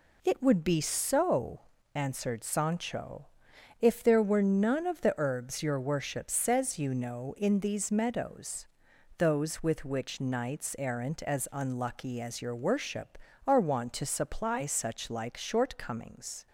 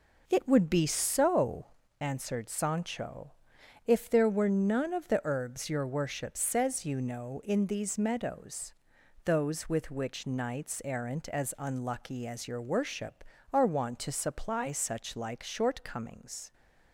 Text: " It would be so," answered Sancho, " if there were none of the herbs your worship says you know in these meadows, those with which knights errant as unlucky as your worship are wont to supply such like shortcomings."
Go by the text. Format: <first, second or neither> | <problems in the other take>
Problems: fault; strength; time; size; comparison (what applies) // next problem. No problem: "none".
first | starts louder than the rest; noticeable; until 1.9 s; 4 dB